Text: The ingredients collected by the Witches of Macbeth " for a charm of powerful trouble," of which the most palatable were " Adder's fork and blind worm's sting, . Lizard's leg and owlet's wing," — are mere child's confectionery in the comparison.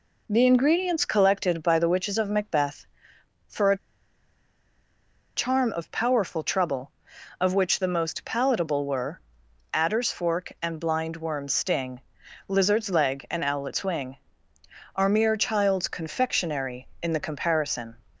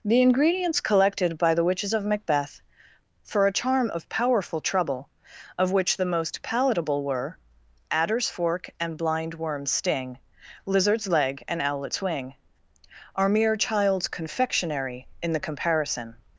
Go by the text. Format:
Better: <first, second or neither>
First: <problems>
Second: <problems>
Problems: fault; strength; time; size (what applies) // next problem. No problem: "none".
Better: second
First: pauses between "a" and "charm"; strong; at 3.7 s; 1.5 s long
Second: none